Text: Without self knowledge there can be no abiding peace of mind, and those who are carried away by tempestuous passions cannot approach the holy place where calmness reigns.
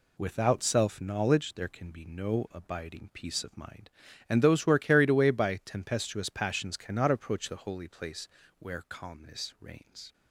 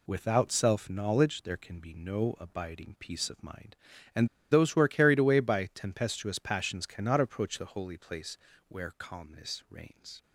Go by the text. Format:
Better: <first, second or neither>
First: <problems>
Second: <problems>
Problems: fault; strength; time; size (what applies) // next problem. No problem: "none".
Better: first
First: pauses between "place" and "where"; slight; at 8.2 s; 0.30 s long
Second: pauses between "and" and "those"; slight; at 4.2 s; 0.24 s long // pauses between "place" and "where"; slight; at 8.3 s; 0.30 s long